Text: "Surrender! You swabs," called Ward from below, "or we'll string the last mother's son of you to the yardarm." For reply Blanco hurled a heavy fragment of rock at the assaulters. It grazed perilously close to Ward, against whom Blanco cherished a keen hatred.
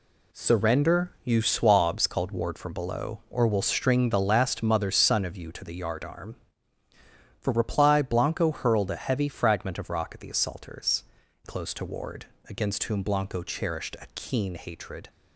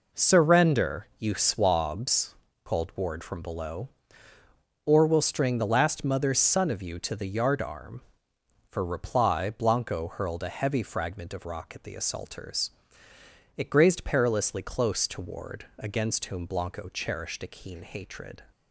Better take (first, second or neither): second